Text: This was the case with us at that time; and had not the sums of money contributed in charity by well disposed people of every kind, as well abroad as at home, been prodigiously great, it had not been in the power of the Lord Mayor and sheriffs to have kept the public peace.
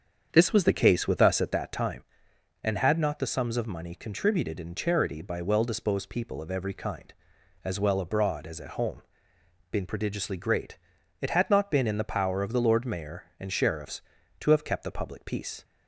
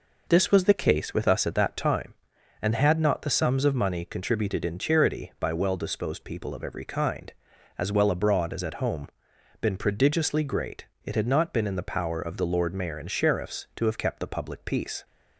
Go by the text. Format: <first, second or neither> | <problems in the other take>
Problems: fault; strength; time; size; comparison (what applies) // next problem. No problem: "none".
second | starts louder than the rest; strong; until 1.7 s; 7.5 dB